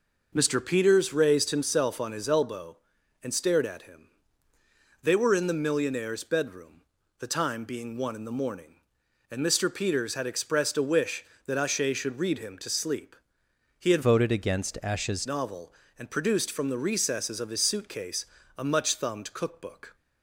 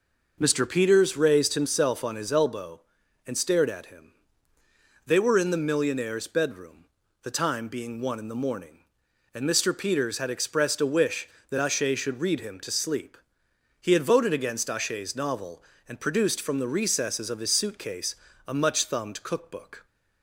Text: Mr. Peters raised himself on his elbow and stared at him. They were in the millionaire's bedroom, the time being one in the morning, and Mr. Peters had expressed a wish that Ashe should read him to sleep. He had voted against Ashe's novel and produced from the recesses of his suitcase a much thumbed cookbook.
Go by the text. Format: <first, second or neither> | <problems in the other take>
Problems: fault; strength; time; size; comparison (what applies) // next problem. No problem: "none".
second | changes voice from "voted" to "Ashe's"; from 14.0 to 15.2 s; 1.2 s long // pauses between "suitcase" and "a"; slight; at 18.2 s; 0.30 s long; slight in the second